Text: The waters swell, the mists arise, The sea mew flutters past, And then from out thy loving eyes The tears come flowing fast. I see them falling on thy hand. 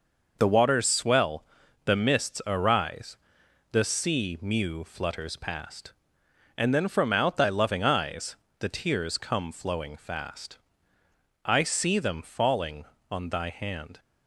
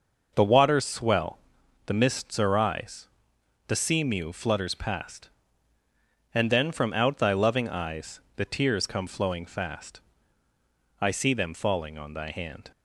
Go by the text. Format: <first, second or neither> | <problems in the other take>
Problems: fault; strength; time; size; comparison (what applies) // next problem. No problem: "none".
neither | pauses between "eyes" and "The"; slight; the same in both